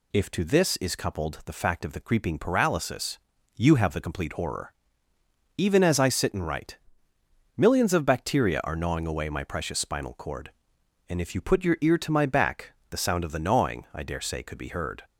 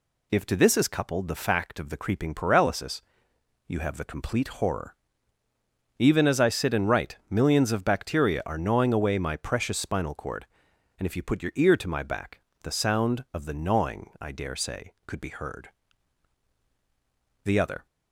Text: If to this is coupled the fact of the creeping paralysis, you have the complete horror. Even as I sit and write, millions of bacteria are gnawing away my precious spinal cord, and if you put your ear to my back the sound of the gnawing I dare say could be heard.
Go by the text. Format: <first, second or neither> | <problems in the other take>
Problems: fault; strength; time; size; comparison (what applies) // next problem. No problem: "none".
first | pauses between "back" and "the"; slight; at 12.3 s; 0.22 s long; slight in the first // goes on to say "The other"; slight; from 17.4 s on; 0.40 s long